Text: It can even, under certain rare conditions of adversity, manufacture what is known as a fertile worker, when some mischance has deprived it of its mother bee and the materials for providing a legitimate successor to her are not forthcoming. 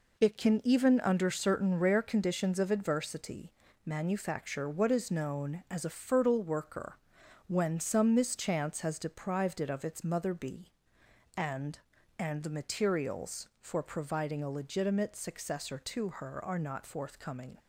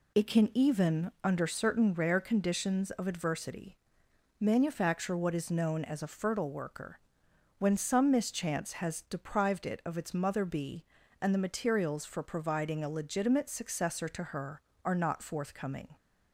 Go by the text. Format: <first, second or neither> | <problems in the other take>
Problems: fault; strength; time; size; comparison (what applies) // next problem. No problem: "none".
second | says "and" twice; at 12.1 s